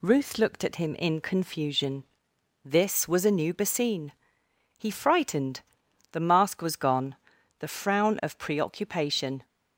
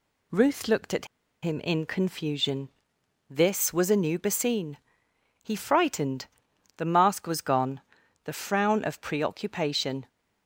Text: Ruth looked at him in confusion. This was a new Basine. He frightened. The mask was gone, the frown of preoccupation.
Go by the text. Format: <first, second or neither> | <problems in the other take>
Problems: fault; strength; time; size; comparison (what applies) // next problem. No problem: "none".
first | pauses between "at" and "him"; at 1.0 s; 0.36 s long